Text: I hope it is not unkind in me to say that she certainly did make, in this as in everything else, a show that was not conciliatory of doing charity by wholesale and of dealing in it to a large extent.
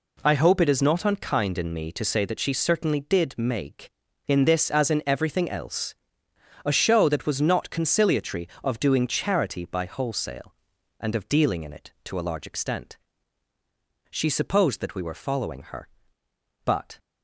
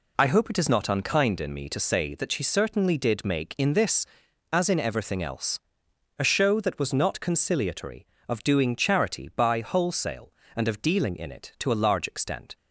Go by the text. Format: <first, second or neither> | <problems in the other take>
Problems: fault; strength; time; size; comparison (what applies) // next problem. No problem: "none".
second | goes on to say "She supposed that we were following her but"; strong; from 14.1 s on; 2.8 s long